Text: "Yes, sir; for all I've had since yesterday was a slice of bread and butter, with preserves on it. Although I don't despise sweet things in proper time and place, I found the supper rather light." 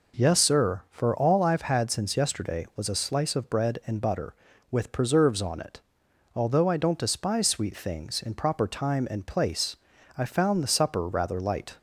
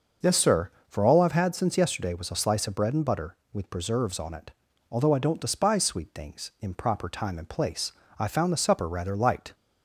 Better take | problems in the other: neither | none

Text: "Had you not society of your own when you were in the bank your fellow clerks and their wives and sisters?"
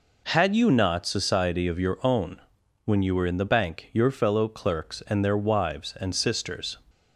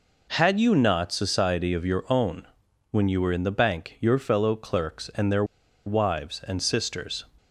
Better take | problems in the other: first | pauses between "own" and "when"; at 2.4 s; 0.44 s long; also in the first // pauses between "their" and "wives"; at 5.4 s; 0.42 s long

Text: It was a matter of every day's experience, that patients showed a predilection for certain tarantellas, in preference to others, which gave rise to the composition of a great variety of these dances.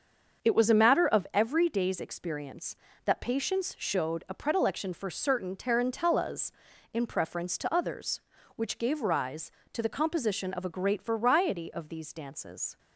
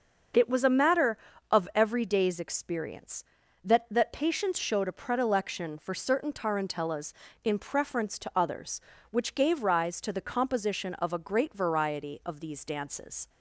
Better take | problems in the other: first | starts louder than the rest; noticeable; until 1.6 s; 6 dB; also in the first // says "that" twice; at 3.8 s

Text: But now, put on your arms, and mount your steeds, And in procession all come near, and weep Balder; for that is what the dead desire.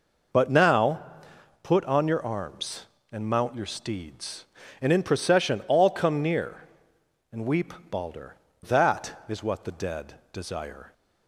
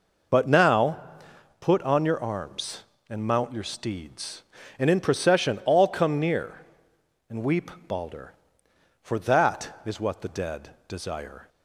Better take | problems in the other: second | pauses between "weep" and "Balder"; slight; at 7.7 s; 0.18 s long; slight in the second // skips "for"; at 8.4 s // pauses between "dead" and "desire"; slight; at 10.1 s; 0.18 s long; slight in the second

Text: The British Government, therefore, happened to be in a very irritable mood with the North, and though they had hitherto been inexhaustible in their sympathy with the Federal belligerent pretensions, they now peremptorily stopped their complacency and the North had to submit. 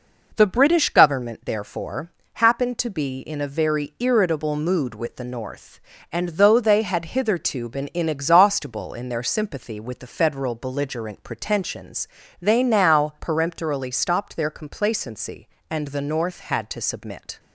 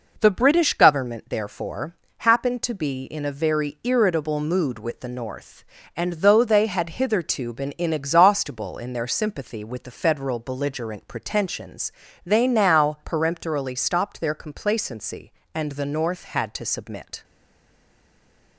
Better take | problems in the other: first | stays silent after the last word; noticeable; from 17.2 s on; 1.3 s long

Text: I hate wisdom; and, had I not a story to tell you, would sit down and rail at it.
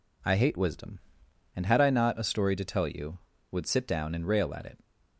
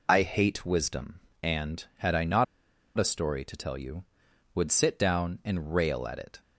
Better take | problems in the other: first | pauses between "not" and "a"; noticeable; at 2.4 s; 0.52 s long

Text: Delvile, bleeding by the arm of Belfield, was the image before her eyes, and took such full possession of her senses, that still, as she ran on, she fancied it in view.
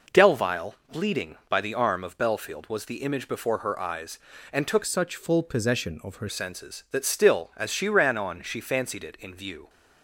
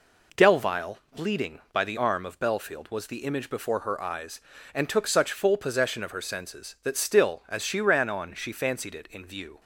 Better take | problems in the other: second | changes voice from "such" to "her"; from 4.8 to 6.2 s; 1.4 s long

